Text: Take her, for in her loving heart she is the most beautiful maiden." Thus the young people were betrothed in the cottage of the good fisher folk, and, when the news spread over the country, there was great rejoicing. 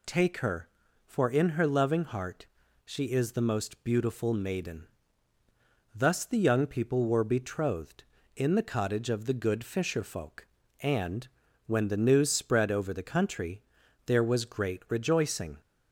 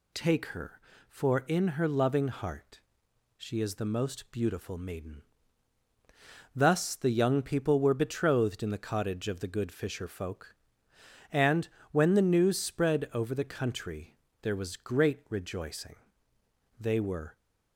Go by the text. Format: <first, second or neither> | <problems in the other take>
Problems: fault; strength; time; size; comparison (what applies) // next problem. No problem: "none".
first | pauses between "heart" and "she"; noticeable; at 2.8 s; 0.56 s long; also in the first // goes on to say "They were"; from 16.7 s on; 0.58 s long